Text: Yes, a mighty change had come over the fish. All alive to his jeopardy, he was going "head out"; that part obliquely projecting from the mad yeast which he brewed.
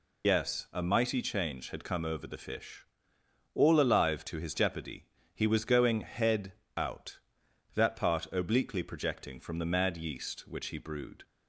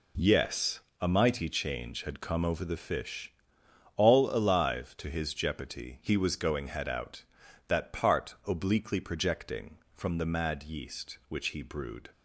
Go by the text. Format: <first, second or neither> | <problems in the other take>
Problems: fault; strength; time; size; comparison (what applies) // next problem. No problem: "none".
second | loses the start of "Yes"; at 0.2 s; 80 ms // pauses between "head" and "out"; slight; at 6.5 s; 0.22 s long